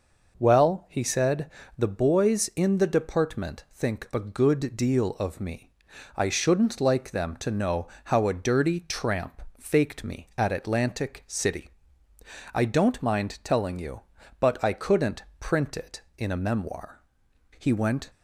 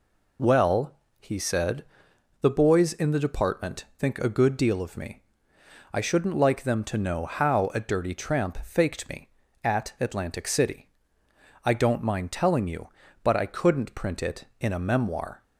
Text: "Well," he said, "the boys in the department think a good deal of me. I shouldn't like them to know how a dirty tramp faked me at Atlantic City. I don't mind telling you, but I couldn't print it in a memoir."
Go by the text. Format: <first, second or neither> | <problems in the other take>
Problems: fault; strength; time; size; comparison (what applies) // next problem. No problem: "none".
second | pauses between "know" and "how"; slight; at 7.8 s; 0.20 s long // pauses between "tramp" and "faked"; slight; at 9.4 s; 0.18 s long // pauses between "couldn't" and "print"; slight; at 15.2 s; 0.16 s long // goes on to say "He went"; from 17.5 s on; 0.50 s long